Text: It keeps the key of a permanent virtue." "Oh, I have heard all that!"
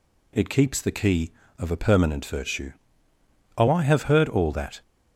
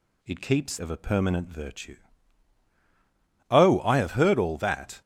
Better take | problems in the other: first | skips "the key"; at 0.7 s

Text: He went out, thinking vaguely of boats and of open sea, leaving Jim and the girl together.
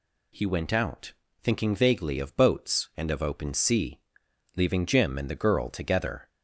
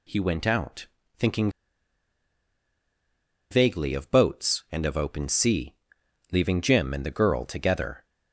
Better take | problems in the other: first | pauses between "thinking" and "vaguely"; strong; at 1.5 s; 1.9 s long

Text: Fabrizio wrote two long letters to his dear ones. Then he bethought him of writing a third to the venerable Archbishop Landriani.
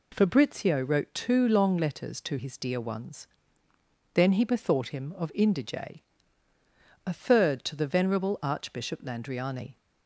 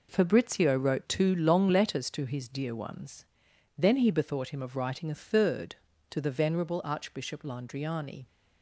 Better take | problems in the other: second | says "indige" for "writing"; at 5.3 s

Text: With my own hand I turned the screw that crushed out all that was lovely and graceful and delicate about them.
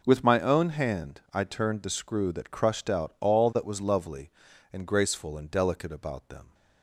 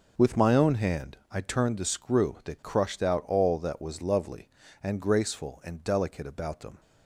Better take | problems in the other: neither | none

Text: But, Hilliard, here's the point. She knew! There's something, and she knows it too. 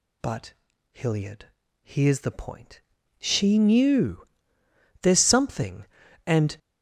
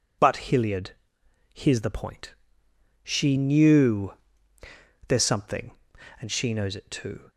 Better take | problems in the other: second | stops before "she knows it too"; at 6.5 s

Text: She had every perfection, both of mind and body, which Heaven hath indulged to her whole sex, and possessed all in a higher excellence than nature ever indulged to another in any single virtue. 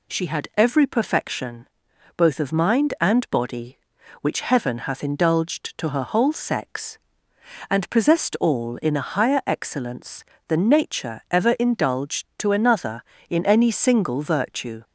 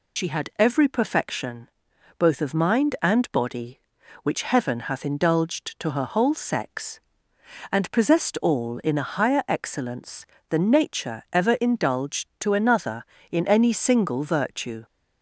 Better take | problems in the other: first | loses the start of "She"; at 0.1 s; 50 ms

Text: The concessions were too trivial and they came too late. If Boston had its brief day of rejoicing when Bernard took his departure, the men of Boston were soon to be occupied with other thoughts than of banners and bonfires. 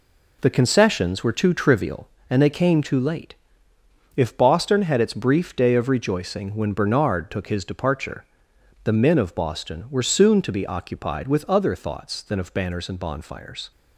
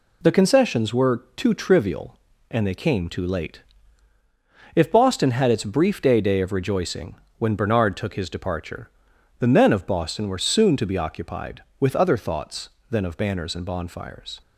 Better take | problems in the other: first | says "day" twice; at 6.1 s // pauses between "rejoicing" and "when"; slight; at 7.1 s; 0.22 s long

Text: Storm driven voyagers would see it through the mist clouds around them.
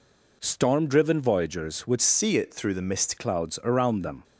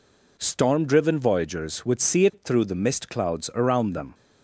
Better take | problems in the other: second | changes voice from "see" to "mist"; from 2.0 to 3.1 s; 1.1 s long

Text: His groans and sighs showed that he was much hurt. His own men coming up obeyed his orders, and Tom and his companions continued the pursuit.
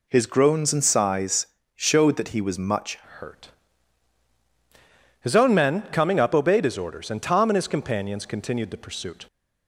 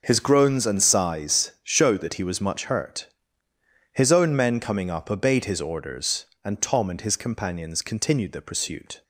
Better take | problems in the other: second | pauses between "sighs" and "showed"; slight; at 1.4 s; 0.28 s long // changes voice at "hurt"; from 3.1 s on; 6.1 s long

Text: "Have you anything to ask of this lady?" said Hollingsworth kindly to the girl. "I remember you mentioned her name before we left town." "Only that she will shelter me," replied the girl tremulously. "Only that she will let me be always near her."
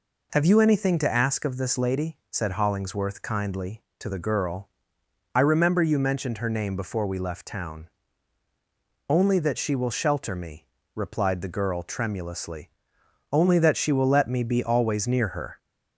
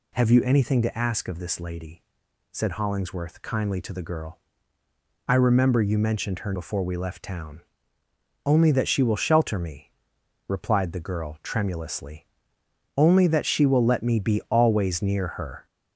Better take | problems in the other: first | skips "name"; at 6.5 s

